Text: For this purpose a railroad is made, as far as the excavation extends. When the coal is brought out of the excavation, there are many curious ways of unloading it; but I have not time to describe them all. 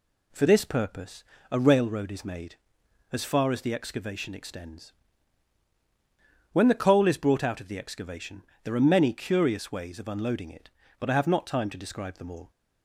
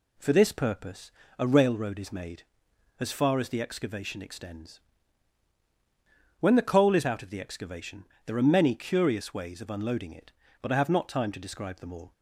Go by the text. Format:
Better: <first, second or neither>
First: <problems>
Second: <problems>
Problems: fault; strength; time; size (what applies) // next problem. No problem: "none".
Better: first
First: pauses between "purpose" and "a"; slight; at 1.2 s; 0.26 s long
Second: pauses between "purpose" and "a"; slight; at 1.1 s; 0.26 s long // skips "brought"; at 7.0 s